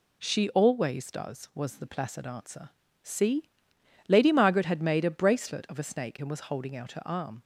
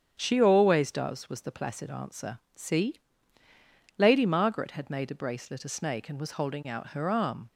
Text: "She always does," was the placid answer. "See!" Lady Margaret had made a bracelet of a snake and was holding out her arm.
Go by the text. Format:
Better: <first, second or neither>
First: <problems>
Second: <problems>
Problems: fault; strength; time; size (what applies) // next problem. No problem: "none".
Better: first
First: none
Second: starts louder than the rest; strong; until 1.1 s; 8 dB // skips "of"; at 5.6 s